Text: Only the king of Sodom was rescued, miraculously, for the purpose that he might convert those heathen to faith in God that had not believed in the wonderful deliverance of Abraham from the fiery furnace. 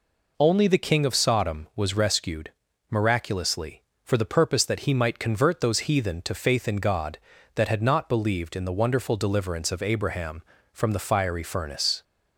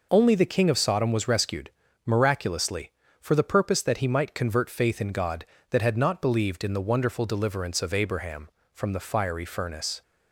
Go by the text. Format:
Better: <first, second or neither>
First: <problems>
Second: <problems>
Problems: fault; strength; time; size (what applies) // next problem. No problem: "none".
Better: first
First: none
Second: skips "those heathen to"; at 4.6 s